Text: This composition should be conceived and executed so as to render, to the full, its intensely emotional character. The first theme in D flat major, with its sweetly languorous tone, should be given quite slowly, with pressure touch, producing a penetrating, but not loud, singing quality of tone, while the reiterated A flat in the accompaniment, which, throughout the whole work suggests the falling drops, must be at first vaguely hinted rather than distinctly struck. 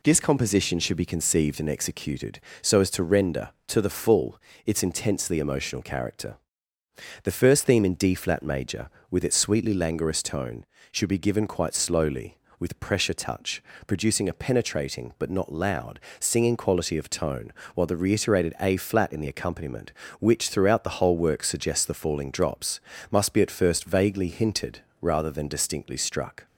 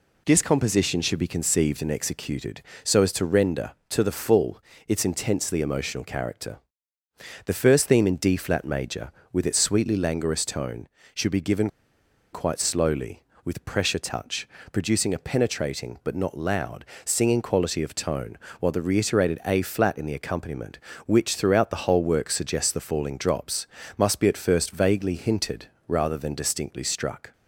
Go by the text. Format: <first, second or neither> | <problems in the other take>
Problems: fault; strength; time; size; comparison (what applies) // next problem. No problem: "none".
first | pauses between "given" and "quite"; noticeable; at 11.6 s; 0.65 s long // pauses between "hinted" and "rather"; slight; at 25.6 s; 0.22 s long; slight in the first